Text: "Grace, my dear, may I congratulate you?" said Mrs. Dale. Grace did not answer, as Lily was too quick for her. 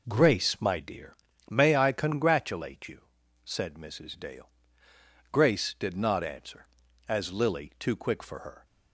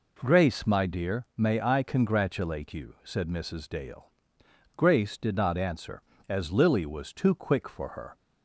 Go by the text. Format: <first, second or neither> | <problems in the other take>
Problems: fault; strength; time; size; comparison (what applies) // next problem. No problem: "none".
second | skips "was"; at 7.7 s